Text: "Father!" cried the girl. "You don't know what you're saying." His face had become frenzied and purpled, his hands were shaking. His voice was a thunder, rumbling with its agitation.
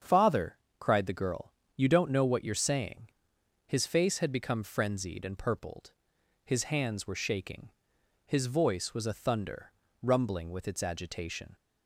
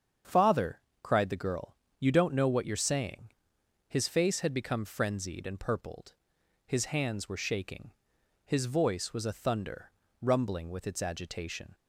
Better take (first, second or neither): neither